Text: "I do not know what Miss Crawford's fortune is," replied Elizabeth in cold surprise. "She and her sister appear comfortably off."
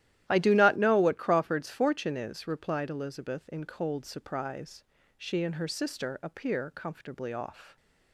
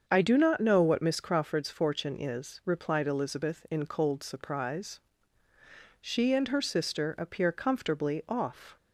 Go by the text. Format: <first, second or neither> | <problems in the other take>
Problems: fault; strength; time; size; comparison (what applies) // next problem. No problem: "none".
second | starts louder than the rest; strong; until 1.2 s; 13 dB; also in the second // skips "Miss"; at 1.1 s